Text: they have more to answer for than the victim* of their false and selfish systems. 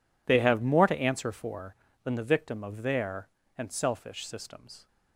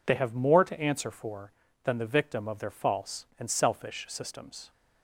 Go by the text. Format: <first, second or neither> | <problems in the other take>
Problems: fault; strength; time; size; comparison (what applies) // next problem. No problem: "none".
second | skips "false"; at 3.4 s